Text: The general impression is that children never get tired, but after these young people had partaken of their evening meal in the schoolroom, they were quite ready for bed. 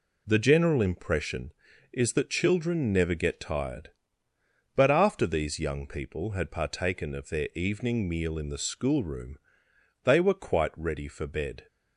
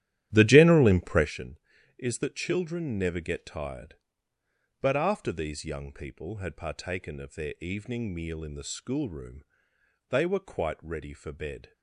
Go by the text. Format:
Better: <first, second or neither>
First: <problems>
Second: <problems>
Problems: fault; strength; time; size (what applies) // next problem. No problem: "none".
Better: first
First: none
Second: starts louder than the rest; strong; until 1.3 s; 12.5 dB